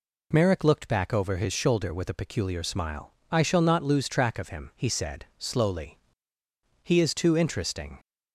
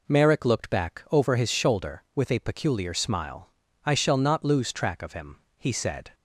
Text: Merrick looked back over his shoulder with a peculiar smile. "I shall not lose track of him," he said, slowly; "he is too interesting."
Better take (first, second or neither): first